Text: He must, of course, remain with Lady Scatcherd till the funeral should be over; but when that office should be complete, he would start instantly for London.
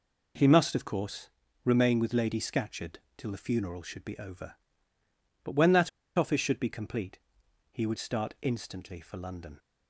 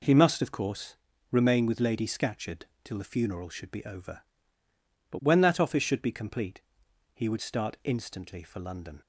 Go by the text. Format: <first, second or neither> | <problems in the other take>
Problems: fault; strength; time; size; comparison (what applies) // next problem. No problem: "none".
second | pauses between "Scatcherd" and "till"; slight; at 2.9 s; 0.18 s long; slight in the second // pauses between "that" and "office"; slight; at 5.8 s; 0.26 s long